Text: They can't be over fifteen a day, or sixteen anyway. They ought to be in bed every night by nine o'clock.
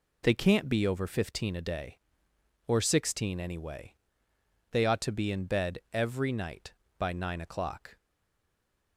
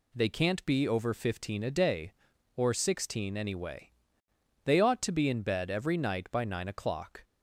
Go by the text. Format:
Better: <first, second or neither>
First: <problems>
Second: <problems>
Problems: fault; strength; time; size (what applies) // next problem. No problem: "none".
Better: second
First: stays silent after the last word; from 7.9 s on; 1.0 s long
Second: none